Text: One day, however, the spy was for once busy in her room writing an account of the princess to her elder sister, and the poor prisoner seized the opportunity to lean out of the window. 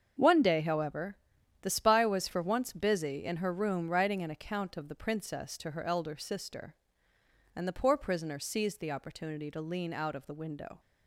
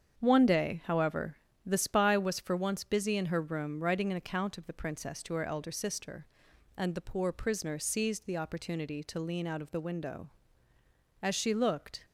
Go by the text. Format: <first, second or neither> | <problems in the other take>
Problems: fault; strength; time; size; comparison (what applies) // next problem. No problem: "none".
first | starts louder than the rest; strong; until 1.2 s; 7.5 dB; also in the first // goes on to say "As she looked"; noticeable; from 11.2 s on; 0.84 s long